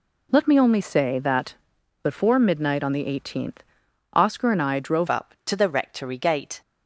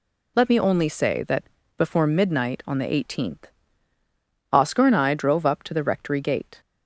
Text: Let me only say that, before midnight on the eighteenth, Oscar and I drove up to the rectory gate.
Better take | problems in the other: second | changes voice at "up"; from 5.0 s on; 1.6 s long

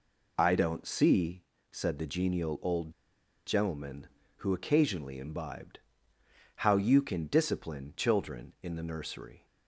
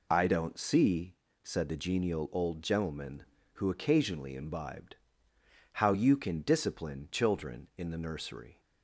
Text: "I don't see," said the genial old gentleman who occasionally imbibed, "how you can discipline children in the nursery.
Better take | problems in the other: second | pauses between "old" and "gentleman"; noticeable; at 2.9 s; 0.55 s long

